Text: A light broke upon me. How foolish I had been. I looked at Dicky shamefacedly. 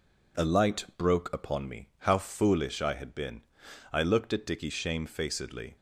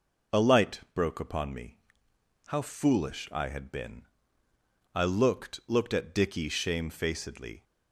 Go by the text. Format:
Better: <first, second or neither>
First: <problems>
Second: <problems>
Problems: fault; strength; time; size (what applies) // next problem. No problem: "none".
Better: first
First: none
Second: says "looked" twice; at 5.6 s